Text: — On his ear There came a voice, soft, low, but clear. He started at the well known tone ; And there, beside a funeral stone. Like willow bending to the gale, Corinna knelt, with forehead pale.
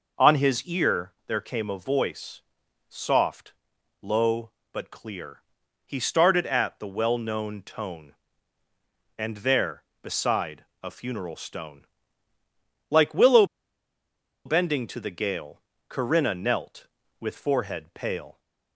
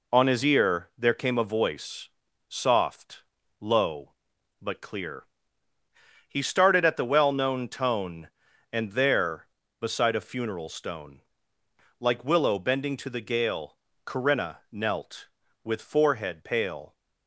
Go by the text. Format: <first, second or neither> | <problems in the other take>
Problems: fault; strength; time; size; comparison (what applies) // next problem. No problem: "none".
second | pauses between "beside" and "a"; slight; at 10.6 s; 0.20 s long // pauses between "willow" and "bending"; at 13.4 s; 1.0 s long